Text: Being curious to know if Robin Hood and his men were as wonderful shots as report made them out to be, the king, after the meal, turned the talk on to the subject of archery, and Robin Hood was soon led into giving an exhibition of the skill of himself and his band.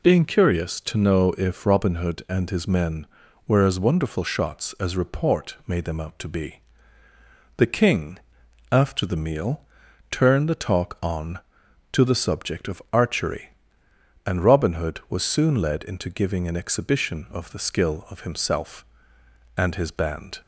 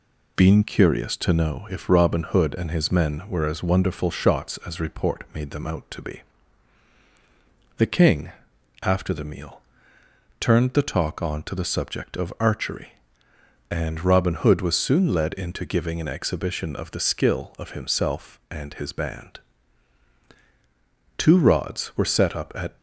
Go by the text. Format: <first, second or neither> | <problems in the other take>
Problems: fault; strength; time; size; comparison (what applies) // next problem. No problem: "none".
first | goes on to say "Two rods were set up at"; from 21.1 s on; 1.6 s long